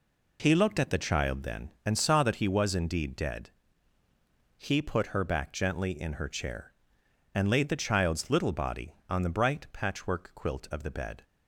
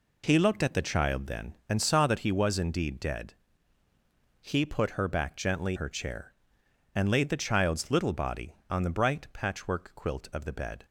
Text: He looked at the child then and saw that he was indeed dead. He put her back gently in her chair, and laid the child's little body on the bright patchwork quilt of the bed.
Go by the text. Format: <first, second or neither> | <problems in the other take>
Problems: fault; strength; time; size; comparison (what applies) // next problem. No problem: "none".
first | skips "in"; at 5.7 s